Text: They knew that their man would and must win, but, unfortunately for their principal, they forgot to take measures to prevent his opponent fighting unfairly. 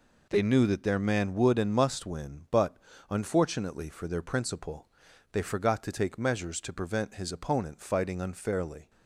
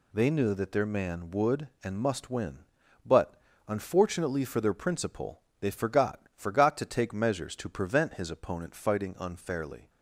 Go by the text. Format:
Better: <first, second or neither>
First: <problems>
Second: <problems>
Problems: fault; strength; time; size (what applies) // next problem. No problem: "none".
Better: first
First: none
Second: says "forgot" twice; at 6.3 s